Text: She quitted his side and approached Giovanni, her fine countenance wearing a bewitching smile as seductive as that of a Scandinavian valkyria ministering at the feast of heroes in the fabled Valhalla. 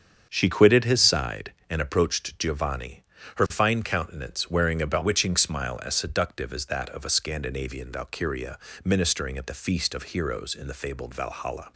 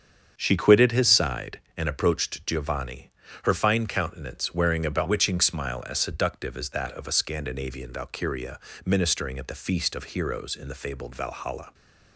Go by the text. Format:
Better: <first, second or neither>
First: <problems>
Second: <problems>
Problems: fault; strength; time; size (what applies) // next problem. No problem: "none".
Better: neither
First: starts louder than the rest; strong; until 1.3 s; 7.5 dB // pauses between "valkyria" and "ministering"; slight; at 8.5 s; 0.26 s long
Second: starts louder than the rest; strong; until 1.3 s; 7.5 dB // pauses between "valkyria" and "ministering"; slight; at 8.5 s; 0.26 s long